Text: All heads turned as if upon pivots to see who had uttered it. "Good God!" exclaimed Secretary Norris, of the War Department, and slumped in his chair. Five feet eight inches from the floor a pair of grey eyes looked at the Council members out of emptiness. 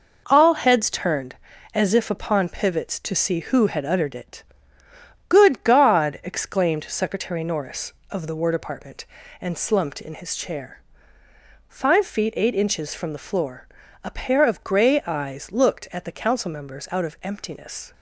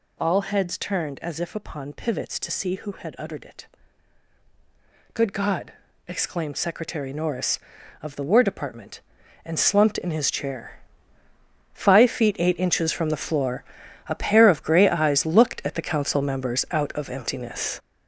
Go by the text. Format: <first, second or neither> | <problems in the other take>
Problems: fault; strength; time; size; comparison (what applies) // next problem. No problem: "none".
first | gets louder; strong; throughout; 7.5 dB // pauses between "floor" and "a"; noticeable; at 13.6 s; 0.46 s long; also in the first